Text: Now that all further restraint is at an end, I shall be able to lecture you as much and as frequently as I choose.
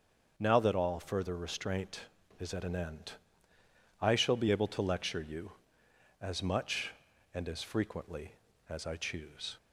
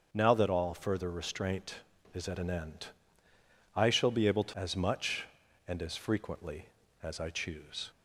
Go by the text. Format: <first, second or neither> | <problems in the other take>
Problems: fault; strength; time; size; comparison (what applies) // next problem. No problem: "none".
first | starts louder than the rest; strong; until 1.1 s; 7 dB; also in the first // skips "lecture you"; at 4.5 s